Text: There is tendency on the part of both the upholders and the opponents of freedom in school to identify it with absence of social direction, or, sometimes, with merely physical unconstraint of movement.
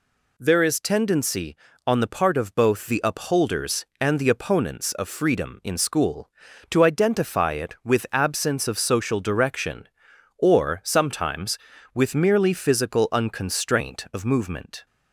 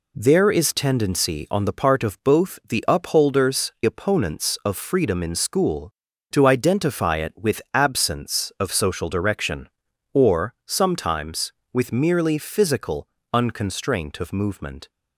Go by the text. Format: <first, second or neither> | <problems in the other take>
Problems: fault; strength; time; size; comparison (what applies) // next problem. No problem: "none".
first | skips "and the"; at 3.7 s // pauses between "physical" and "unconstraint"; slight; at 13.0 s; 0.24 s long